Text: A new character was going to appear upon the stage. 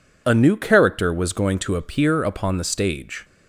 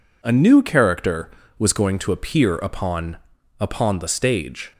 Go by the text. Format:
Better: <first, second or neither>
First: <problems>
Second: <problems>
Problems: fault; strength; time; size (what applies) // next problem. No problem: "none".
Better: first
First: none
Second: says "upon" twice; at 3.5 s